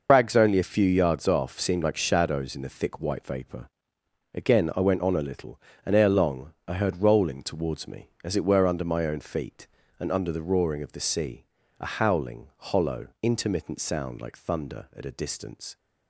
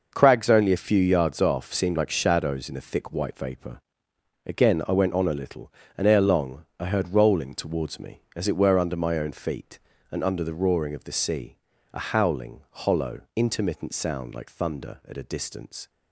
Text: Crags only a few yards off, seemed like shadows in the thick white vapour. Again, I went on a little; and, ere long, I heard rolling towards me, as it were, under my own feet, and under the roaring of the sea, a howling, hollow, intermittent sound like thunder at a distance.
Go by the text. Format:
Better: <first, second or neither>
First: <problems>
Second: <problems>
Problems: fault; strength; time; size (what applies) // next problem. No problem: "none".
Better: second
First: loses the start of "Crags"; at 0.0 s; 90 ms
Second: none